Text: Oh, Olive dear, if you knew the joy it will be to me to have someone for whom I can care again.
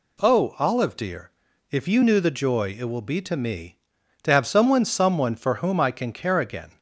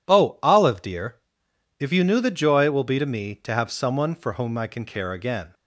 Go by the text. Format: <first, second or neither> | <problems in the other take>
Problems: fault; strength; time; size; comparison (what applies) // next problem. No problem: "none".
second | says "someone" twice; at 4.8 s